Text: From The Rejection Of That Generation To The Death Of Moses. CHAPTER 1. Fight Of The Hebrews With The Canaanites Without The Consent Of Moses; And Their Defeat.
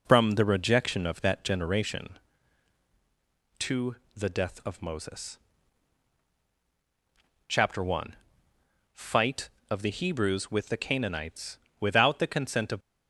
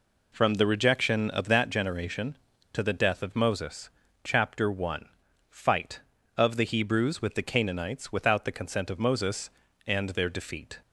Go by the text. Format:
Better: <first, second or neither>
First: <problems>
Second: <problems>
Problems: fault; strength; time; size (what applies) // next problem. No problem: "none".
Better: second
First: pauses between "To" and "The"; slight; at 3.9 s; 0.20 s long // pauses between "Canaanites" and "Without"; slight; at 11.5 s; 0.22 s long // stops before "Moses And Their Defeat"; at 12.8 s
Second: none